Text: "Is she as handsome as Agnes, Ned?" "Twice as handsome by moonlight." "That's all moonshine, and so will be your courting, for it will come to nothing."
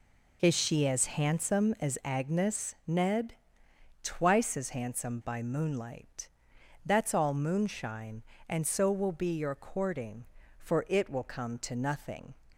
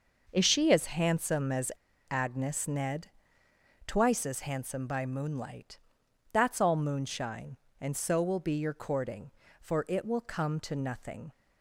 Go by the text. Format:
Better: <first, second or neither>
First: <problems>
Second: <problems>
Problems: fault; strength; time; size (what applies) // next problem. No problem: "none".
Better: first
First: none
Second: pauses between "as" and "Agnes"; at 1.7 s; 0.38 s long